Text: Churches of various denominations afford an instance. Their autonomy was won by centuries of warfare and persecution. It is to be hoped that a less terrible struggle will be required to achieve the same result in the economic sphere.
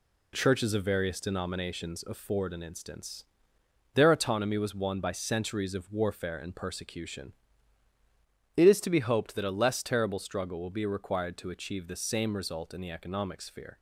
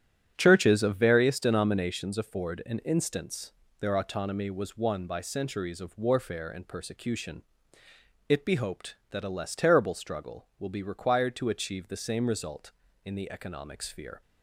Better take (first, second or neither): first